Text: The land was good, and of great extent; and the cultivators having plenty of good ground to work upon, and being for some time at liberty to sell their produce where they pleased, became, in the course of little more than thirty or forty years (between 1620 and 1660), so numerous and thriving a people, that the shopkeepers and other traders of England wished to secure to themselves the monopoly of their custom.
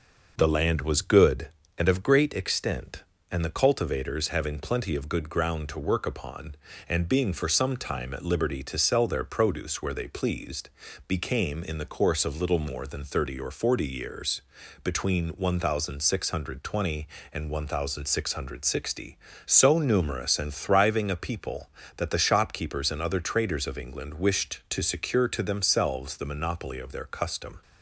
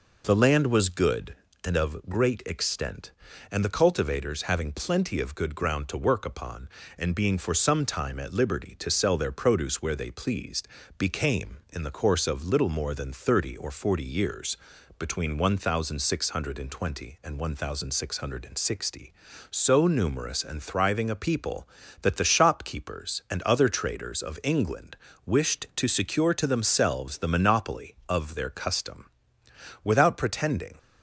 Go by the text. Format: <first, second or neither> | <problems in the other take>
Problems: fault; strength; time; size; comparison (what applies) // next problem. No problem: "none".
first | pauses between "England" and "wished"; slight; at 24.9 s; 0.28 s long // goes on to say "Without pretending"; noticeable; from 29.8 s on; 0.94 s long